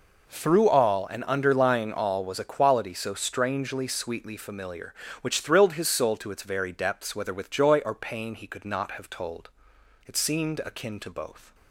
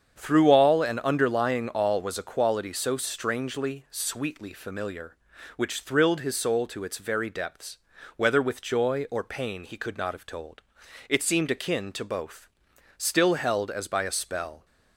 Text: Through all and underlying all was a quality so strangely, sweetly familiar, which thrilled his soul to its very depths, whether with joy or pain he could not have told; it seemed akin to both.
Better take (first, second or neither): first